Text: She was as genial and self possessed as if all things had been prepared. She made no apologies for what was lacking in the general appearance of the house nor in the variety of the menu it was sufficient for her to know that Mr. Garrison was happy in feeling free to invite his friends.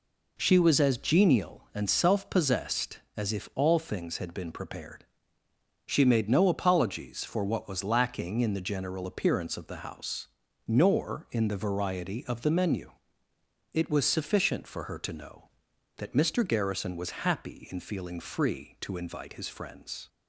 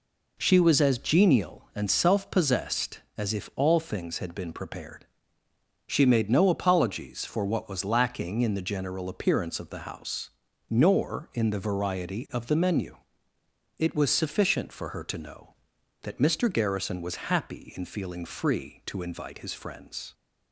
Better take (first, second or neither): neither